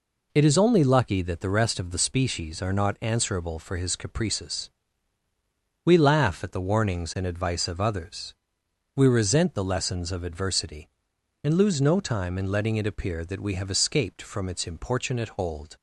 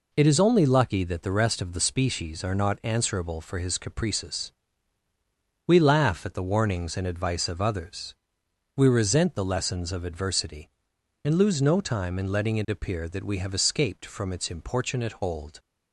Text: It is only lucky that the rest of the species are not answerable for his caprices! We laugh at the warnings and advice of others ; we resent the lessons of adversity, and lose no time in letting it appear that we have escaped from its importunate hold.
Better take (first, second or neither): neither